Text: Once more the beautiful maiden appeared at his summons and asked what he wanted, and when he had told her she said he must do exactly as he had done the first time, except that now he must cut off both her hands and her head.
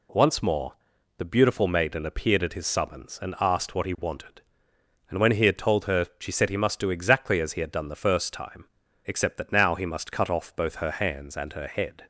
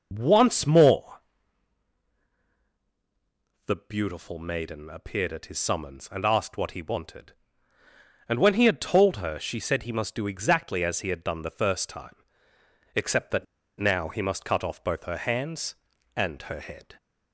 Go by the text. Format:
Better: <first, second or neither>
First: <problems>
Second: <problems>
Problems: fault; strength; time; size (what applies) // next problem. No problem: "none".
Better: first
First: pauses between "more" and "the"; noticeable; at 0.7 s; 0.46 s long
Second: pauses between "more" and "the"; strong; at 1.2 s; 2.4 s long // pauses between "that" and "now"; slight; at 13.4 s; 0.33 s long